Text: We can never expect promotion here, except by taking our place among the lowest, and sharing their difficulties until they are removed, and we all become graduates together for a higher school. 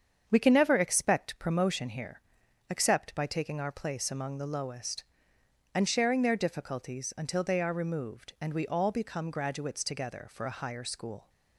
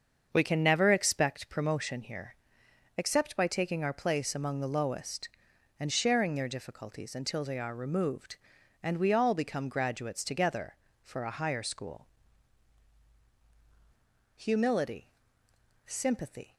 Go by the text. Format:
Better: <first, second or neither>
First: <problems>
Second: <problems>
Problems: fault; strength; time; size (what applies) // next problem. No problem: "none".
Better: first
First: starts louder than the rest; strong; until 1.2 s; 7.5 dB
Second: starts louder than the rest; until 1.3 s; 6.5 dB // goes on to say "Humility Sympathy"; strong; from 14.3 s on; 2.1 s long